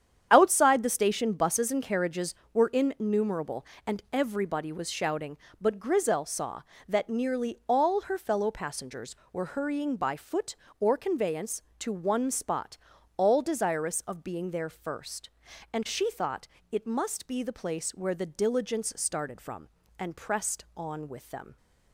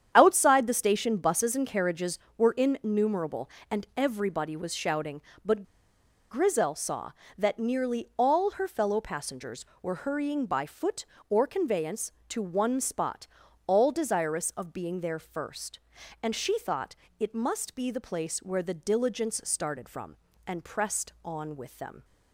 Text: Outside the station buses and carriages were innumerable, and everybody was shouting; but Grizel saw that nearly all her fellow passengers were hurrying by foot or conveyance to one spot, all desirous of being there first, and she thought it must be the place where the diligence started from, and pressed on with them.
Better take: first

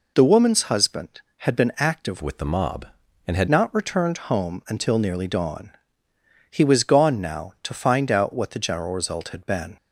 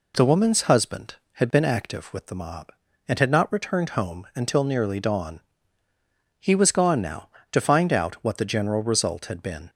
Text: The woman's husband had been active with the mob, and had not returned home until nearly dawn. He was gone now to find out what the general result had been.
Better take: second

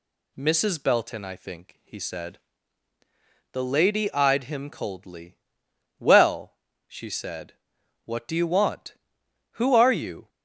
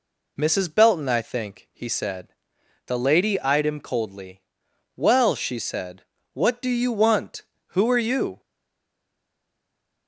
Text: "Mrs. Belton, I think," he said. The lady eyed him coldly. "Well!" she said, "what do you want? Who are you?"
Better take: first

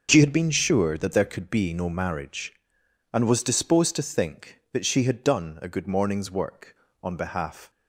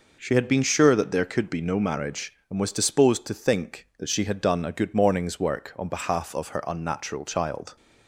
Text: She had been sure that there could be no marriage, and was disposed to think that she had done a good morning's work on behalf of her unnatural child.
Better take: second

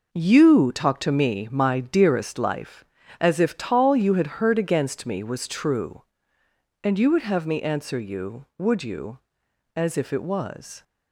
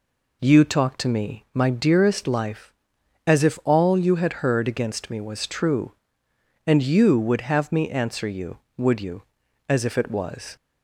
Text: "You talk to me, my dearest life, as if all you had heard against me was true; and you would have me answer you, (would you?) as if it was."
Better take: second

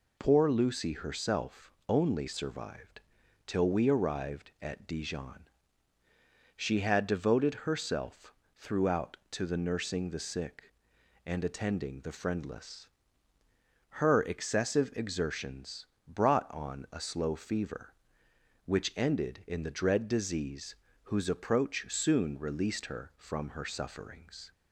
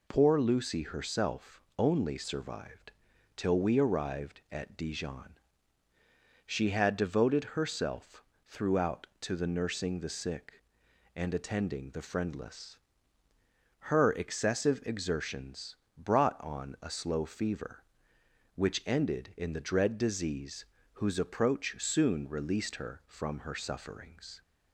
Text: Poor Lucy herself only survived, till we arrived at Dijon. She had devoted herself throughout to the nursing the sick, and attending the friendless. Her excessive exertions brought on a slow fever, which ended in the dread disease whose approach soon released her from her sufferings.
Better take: neither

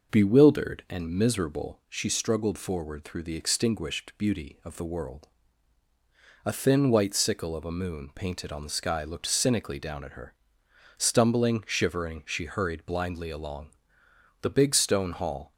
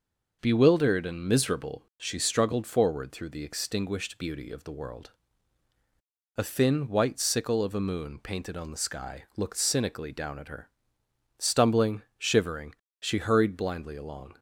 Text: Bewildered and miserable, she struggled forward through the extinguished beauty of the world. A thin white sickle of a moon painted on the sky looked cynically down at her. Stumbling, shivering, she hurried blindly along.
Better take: second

